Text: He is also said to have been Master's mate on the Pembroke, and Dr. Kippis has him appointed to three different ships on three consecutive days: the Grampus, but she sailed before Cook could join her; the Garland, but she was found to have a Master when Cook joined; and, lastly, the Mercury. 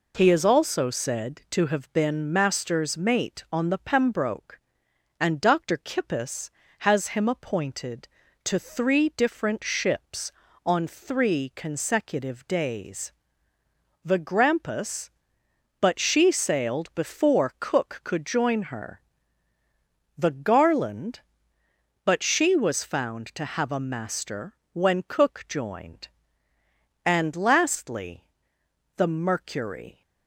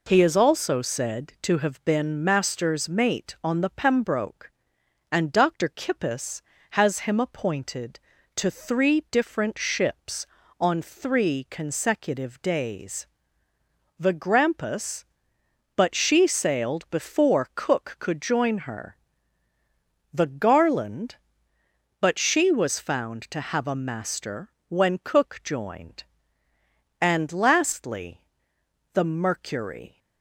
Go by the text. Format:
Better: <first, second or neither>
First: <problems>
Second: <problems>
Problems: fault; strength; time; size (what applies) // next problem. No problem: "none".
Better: neither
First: pauses between "Master" and "when"; slight; at 24.5 s; 0.18 s long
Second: pauses between "Master" and "when"; slight; at 24.4 s; 0.18 s long